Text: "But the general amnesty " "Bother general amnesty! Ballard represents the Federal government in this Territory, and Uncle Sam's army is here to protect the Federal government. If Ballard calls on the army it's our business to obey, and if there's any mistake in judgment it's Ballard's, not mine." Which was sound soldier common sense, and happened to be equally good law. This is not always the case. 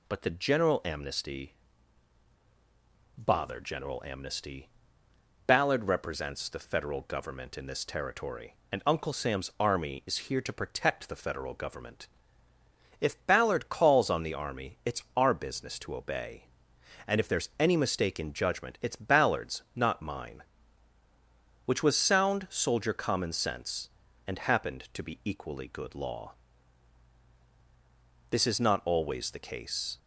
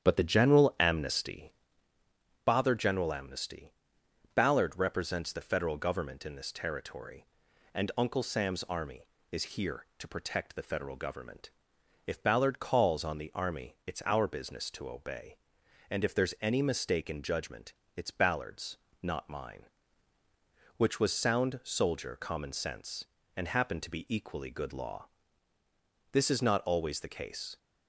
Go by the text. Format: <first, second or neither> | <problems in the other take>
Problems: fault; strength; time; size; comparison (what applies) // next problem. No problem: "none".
first | starts louder than the rest; strong; until 1.7 s; 7.5 dB // pauses between "judgment" and "it's"; slight; at 17.7 s; 0.22 s long